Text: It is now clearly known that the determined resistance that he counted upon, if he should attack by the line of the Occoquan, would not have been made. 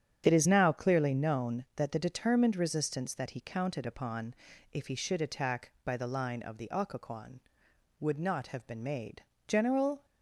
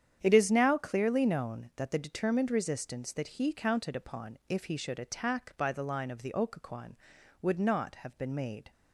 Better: second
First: starts louder than the rest; strong; until 1.2 s; 9 dB // goes on to say "General"; from 9.4 s on; 0.56 s long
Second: starts louder than the rest; strong; until 1.2 s; 9 dB

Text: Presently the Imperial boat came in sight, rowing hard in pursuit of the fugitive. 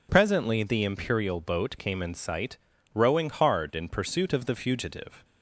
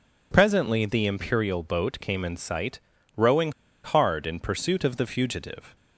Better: first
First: none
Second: pauses between "rowing" and "hard"; slight; at 3.5 s; 0.31 s long

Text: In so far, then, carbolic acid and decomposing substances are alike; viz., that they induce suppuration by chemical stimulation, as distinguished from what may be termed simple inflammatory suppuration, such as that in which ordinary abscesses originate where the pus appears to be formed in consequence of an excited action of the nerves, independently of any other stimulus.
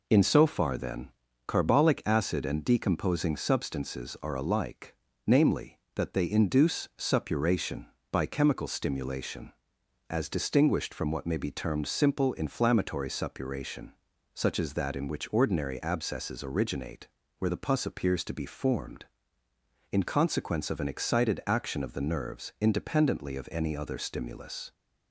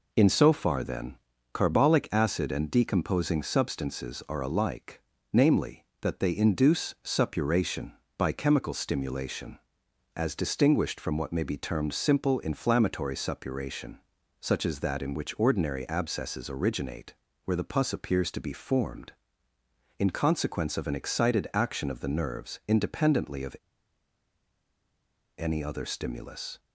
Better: first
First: pauses between "originate" and "where"; slight; at 17.0 s; 0.32 s long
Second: pauses between "originate" and "where"; slight; at 17.1 s; 0.32 s long // pauses between "of" and "any"; strong; at 23.5 s; 1.8 s long

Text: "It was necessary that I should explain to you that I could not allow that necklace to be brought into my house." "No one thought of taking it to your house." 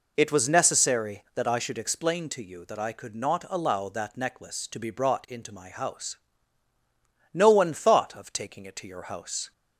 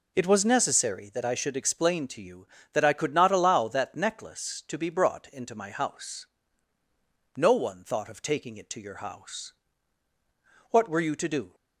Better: first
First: none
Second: goes on to say "What were you to do"; noticeable; from 10.7 s on; 0.84 s long

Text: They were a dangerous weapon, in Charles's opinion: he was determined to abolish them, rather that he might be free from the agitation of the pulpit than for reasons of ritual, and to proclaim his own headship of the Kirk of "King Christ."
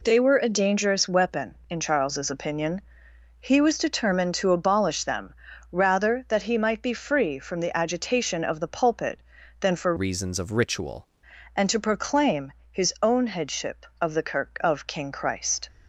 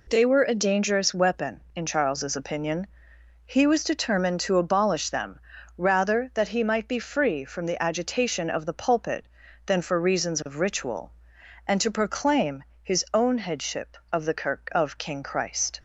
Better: second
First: changes voice from "reasons" to "ritual"; from 9.9 to 11.0 s; 1.1 s long // pauses between "proclaim" and "his"; slight; at 12.5 s; 0.18 s long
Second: pauses between "proclaim" and "his"; slight; at 12.6 s; 0.18 s long

